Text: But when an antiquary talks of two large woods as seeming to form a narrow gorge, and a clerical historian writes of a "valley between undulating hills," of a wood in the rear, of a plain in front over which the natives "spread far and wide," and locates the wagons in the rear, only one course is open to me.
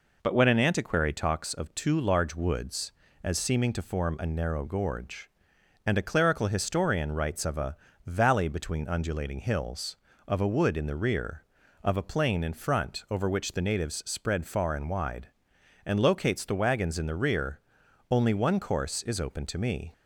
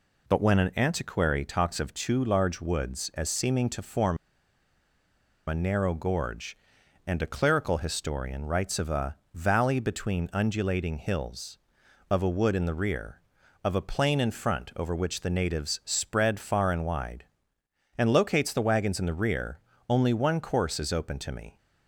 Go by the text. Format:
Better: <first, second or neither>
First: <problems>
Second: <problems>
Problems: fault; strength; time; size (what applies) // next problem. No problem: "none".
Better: first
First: pauses between "a" and "valley"; slight; at 7.7 s; 0.28 s long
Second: pauses between "form" and "a"; strong; at 4.1 s; 1.3 s long // pauses between "a" and "valley"; slight; at 9.1 s; 0.18 s long